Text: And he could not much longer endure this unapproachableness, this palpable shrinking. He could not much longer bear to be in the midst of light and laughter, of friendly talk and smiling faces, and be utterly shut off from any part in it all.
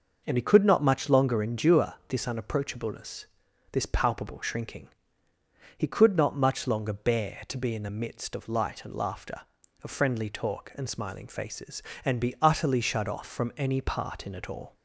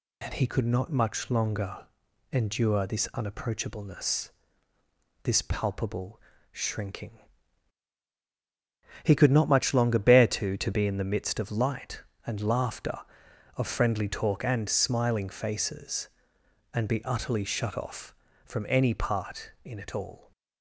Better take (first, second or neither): first